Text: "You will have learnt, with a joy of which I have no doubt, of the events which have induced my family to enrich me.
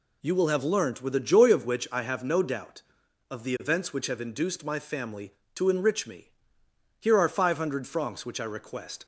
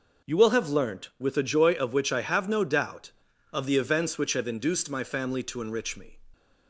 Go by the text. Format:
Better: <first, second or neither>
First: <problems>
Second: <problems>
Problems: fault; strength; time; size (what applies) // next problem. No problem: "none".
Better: second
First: goes on to say "Here are five hundred francs which I request"; strong; from 7.0 s on; 2.0 s long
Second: none